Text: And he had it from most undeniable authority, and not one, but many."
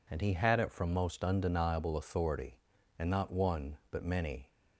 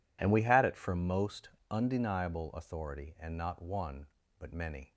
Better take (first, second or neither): first